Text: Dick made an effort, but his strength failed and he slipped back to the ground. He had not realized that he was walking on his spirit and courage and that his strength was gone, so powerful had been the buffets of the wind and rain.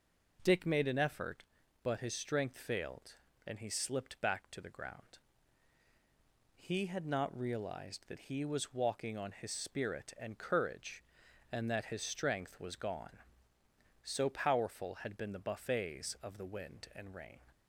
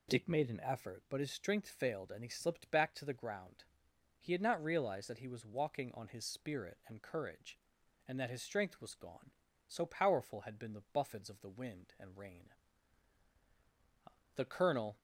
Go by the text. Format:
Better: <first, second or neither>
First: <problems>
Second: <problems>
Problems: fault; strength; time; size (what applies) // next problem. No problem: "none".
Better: first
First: none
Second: goes on to say "The colonel"; noticeable; from 14.3 s on; 0.62 s long